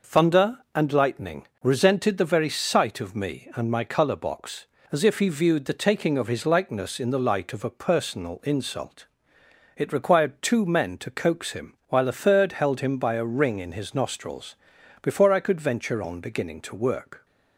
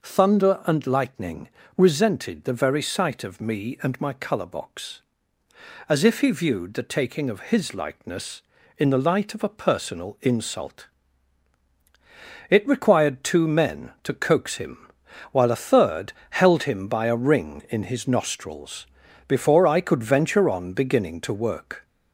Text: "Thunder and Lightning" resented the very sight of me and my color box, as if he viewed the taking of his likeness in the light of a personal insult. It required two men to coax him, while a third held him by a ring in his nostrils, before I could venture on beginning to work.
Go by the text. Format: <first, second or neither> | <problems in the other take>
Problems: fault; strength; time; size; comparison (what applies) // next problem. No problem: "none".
first | gets louder; slight; throughout; 2.5 dB // pauses between "Lightning" and "resented"; slight; at 1.4 s; 0.28 s long; slight in the first // pauses between "third" and "held"; slight; at 16.1 s; 0.18 s long